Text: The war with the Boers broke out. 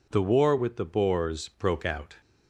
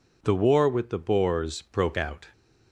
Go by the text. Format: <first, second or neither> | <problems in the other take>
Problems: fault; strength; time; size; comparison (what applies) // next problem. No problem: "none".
neither | none